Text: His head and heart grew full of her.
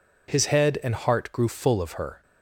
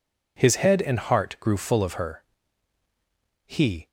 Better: first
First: none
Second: goes on to say "He"; slight; from 3.4 s on; 0.42 s long

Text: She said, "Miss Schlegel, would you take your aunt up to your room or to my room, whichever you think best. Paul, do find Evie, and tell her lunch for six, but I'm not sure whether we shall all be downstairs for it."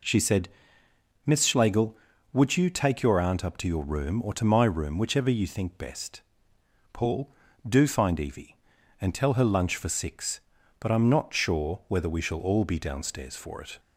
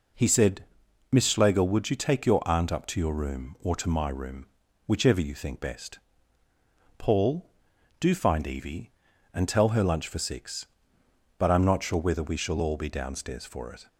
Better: first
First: none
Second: says "He" for "She"; at 0.1 s

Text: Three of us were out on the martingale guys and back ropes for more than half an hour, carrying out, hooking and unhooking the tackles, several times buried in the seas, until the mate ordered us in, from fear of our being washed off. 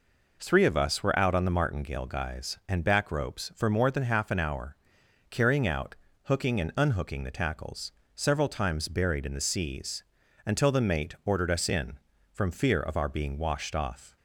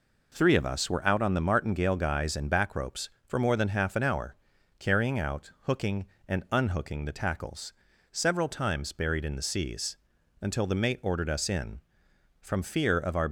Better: first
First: none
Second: stops before "being washed off"; at 13.2 s

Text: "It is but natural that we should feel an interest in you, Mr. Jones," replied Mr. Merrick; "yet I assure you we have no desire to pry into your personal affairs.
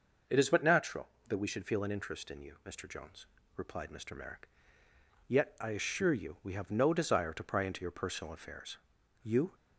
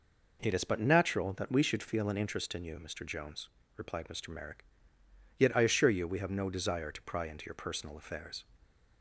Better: second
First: starts louder than the rest; noticeable; until 1.4 s; 6 dB // goes on to say "You"; slight; from 9.2 s on; 0.32 s long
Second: none

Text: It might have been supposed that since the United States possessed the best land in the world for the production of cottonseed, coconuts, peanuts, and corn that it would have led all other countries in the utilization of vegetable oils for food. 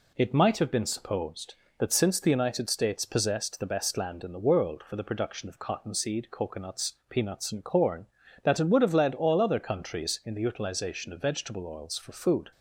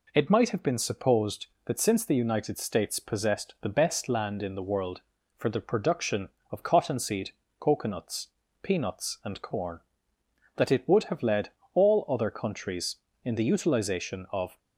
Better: first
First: none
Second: pauses between "led" and "all"; slight; at 11.4 s; 0.24 s long // stops before "vegetable oils for food"; at 14.5 s

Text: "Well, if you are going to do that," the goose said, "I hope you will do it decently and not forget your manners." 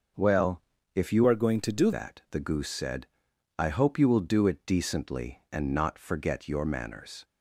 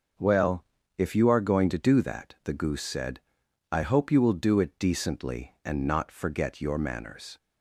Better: second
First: starts louder than the rest; until 1.5 s; 6 dB // changes voice from "are" to "do"; from 1.2 to 1.9 s; 0.7 s long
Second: starts louder than the rest; noticeable; until 1.5 s; 6 dB

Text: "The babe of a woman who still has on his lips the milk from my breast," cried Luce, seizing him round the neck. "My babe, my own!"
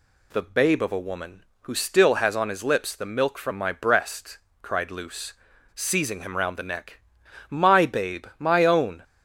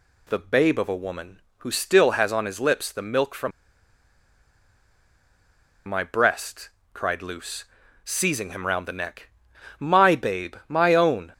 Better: first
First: none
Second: pauses between "from" and "my"; strong; at 3.5 s; 2.3 s long

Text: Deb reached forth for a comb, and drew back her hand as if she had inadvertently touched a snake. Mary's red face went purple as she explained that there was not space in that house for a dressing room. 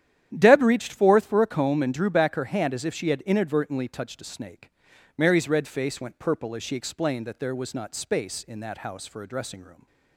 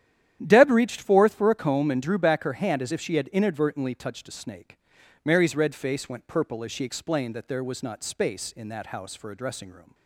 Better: neither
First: starts louder than the rest; strong; until 1.3 s; 10.5 dB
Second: starts louder than the rest; strong; until 1.4 s; 11 dB

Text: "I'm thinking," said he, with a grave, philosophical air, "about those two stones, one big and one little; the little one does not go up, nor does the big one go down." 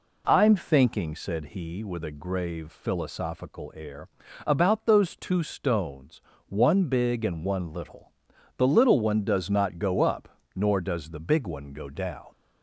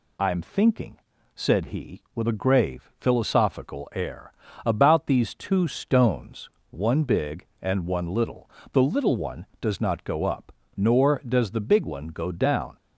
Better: first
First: none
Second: says "these" for "those"; at 5.0 s

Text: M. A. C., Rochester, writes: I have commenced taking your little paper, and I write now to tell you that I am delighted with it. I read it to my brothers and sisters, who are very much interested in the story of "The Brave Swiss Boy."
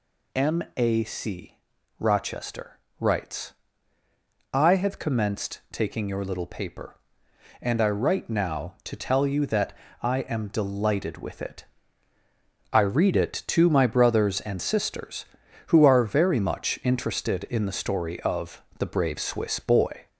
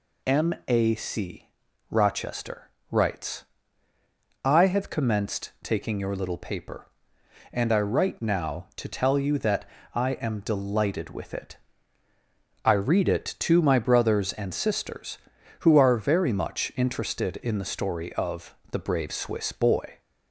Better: second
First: gets louder; slight; throughout; 2.5 dB // pauses between "that" and "I"; slight; at 9.7 s; 0.30 s long // pauses between "of" and "The"; slight; at 18.6 s; 0.18 s long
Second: pauses between "that" and "I"; slight; at 9.6 s; 0.30 s long // pauses between "of" and "The"; slight; at 18.5 s; 0.18 s long

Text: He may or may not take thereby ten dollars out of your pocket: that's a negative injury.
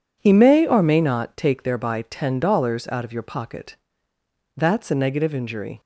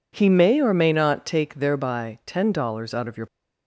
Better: first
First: none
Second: stops before "pocket that's a negative injury"; at 3.2 s

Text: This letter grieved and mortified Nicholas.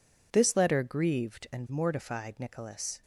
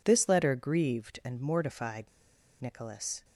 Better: first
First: none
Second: pauses between "mortified" and "Nicholas"; noticeable; at 2.0 s; 0.53 s long

